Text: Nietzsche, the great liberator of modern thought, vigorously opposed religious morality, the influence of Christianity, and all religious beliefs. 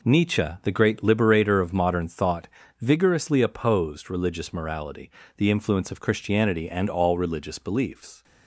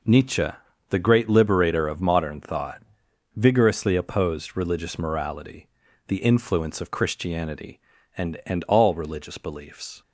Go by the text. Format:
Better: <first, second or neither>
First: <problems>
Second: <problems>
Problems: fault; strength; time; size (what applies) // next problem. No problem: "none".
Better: first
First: none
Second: says "and" twice; at 8.4 s